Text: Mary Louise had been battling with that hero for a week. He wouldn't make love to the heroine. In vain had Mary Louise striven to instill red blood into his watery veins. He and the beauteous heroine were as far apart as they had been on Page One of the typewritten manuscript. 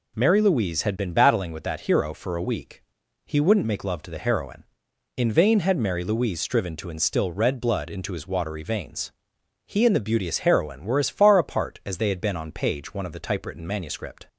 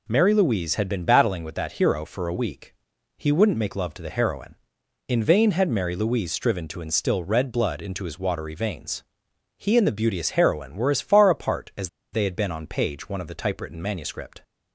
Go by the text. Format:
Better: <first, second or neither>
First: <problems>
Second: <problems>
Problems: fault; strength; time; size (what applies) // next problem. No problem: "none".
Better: first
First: none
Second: pauses between "as" and "they"; slight; at 11.8 s; 0.23 s long